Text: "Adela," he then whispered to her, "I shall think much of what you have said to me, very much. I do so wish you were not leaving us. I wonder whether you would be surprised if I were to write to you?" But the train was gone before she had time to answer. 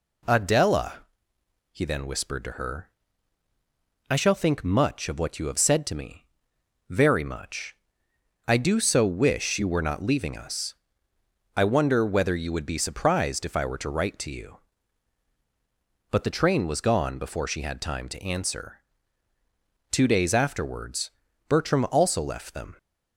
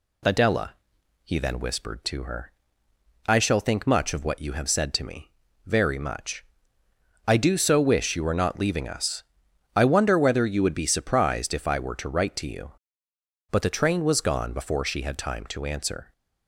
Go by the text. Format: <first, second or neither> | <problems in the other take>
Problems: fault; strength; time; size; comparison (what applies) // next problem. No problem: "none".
second | goes on to say "Two days afterwards Bertram also left them"; strong; from 19.9 s on; 2.8 s long